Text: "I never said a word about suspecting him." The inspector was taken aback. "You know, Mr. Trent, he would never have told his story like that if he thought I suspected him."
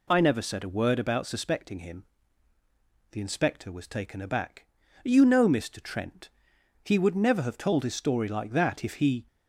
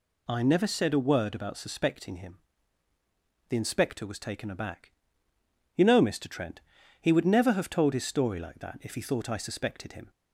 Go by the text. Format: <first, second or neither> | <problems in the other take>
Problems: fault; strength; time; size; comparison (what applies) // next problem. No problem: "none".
second | stops before "thought I suspected him"; at 9.2 s